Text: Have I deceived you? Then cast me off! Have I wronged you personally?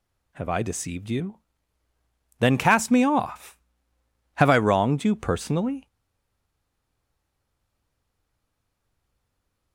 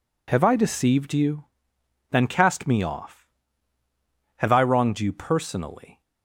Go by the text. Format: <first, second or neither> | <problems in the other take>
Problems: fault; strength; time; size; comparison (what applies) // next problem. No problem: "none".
second | stays silent after the last word; strong; from 5.8 s on; 3.9 s long